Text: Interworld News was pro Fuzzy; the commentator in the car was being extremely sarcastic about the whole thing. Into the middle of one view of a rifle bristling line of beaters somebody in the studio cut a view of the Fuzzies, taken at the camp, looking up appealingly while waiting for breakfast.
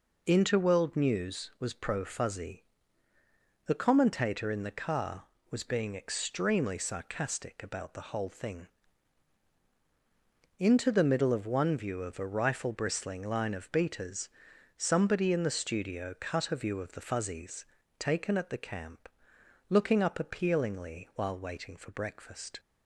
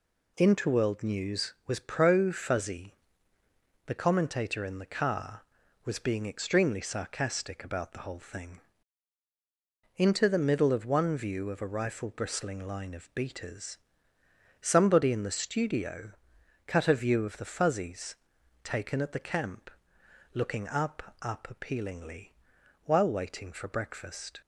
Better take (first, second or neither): first